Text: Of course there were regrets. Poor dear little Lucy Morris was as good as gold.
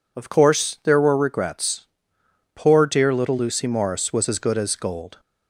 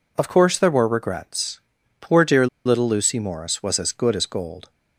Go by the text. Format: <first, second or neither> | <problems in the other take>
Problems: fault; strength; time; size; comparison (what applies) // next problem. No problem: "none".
first | pauses between "dear" and "little"; slight; at 2.4 s; 0.19 s long